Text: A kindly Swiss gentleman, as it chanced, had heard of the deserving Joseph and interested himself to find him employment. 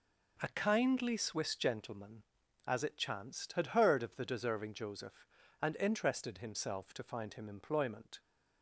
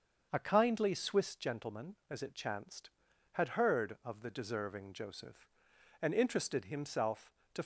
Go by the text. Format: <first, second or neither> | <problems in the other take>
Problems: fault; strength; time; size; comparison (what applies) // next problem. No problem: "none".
first | starts louder than the rest; until 1.3 s; 7 dB // stops before "find him employment"; at 7.6 s